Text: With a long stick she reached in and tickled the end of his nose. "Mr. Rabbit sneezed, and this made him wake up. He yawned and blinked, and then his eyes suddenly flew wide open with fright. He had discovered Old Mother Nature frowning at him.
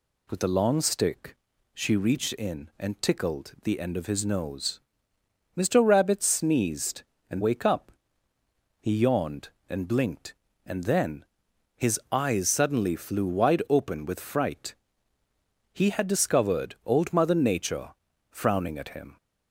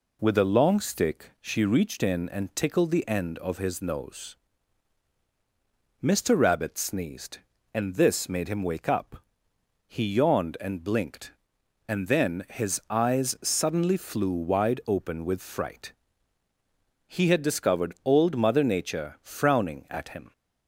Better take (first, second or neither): second